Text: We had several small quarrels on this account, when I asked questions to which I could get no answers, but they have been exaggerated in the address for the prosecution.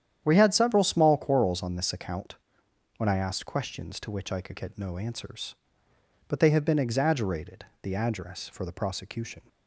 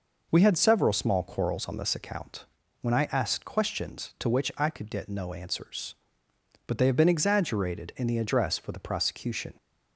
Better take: second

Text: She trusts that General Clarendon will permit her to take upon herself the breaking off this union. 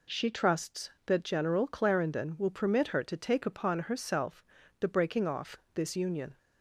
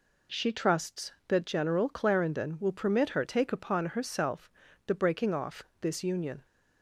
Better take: first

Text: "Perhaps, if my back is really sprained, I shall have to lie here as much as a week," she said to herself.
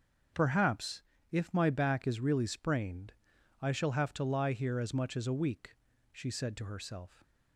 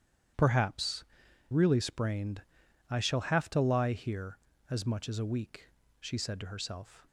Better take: first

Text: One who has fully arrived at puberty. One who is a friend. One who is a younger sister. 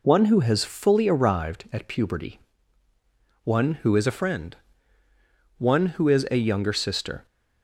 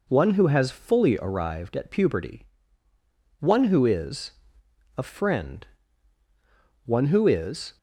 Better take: first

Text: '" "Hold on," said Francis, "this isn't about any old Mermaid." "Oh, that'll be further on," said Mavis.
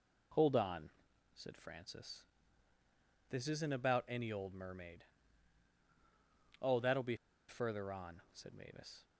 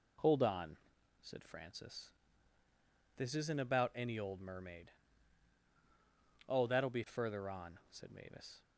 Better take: second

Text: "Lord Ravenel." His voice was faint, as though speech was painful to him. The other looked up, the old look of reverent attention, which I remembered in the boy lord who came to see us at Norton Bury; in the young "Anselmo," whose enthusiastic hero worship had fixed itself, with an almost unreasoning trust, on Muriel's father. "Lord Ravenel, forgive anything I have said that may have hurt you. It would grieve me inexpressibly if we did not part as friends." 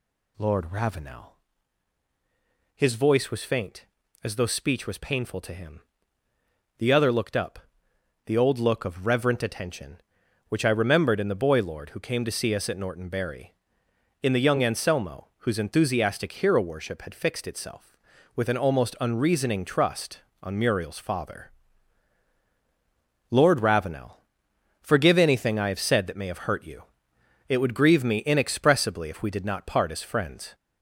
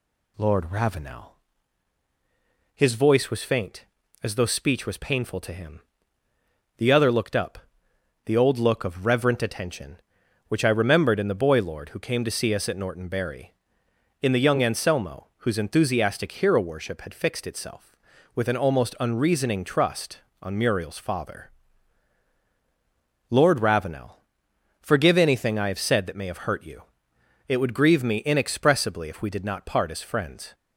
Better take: second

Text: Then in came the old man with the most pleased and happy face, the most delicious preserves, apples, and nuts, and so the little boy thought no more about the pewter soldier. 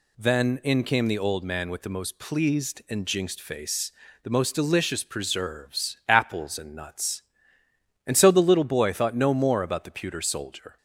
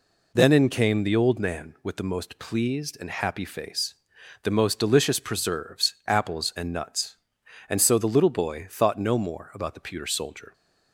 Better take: second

